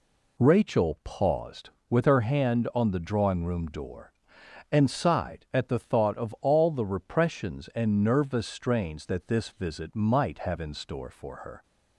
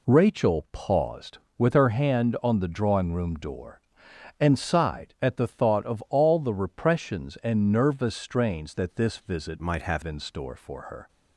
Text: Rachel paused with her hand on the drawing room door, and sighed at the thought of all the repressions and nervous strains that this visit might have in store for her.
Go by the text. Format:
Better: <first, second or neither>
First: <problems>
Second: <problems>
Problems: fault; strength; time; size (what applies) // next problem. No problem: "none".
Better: first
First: none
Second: changes voice from "might" to "have"; from 9.6 to 10.0 s; 0.4 s long